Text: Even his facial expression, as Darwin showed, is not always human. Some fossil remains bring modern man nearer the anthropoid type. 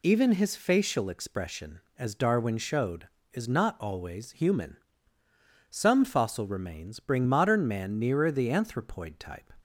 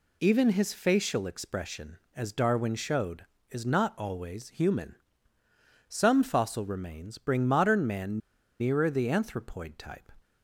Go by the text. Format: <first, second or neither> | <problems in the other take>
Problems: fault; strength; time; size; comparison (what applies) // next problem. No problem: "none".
first | pauses between "man" and "nearer"; at 8.1 s; 0.42 s long